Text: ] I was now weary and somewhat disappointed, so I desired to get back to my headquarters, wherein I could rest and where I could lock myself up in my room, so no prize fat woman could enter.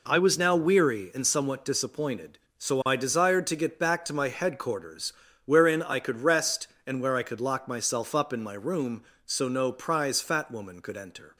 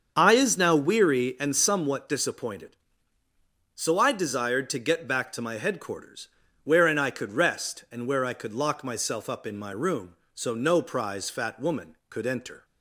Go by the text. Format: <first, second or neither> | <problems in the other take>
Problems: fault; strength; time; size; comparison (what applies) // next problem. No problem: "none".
first | starts louder than the rest; until 1.1 s; 7 dB // says "is" for "was"; at 0.3 s